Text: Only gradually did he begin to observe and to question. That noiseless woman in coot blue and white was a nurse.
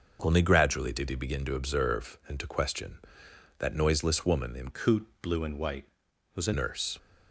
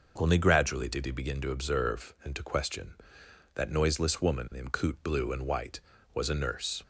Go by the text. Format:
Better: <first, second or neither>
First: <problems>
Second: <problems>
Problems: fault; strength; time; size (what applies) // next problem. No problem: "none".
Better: second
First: starts louder than the rest; until 1.2 s; 6.5 dB // changes voice from "coot" to "a"; from 4.7 to 6.5 s; 1.8 s long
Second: none